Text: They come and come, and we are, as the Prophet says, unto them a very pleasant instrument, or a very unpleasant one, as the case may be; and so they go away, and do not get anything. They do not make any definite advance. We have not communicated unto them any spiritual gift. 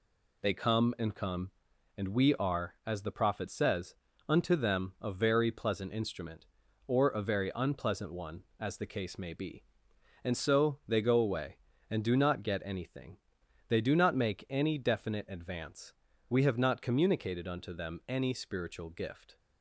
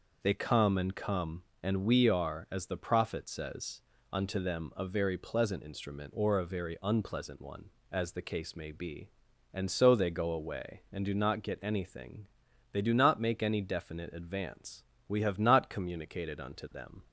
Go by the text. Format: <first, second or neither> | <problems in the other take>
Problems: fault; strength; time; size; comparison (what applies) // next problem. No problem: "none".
first | stops before "any spiritual gift"; at 17.0 s